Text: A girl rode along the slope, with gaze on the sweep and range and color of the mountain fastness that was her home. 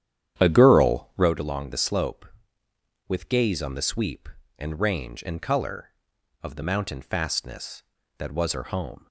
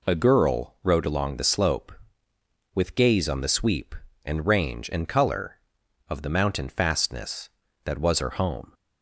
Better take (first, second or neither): second